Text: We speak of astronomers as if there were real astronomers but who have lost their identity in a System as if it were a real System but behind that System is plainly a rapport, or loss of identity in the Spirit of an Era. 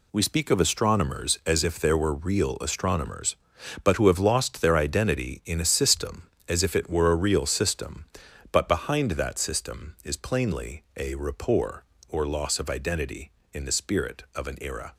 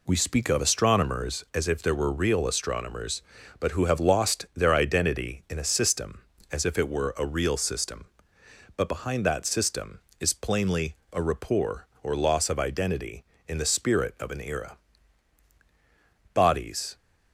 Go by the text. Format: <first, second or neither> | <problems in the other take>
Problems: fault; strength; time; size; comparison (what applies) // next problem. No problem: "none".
first | pauses between "plainly" and "a"; slight; at 10.9 s; 0.16 s long // goes on to say "Bodies"; noticeable; from 16.3 s on; 0.62 s long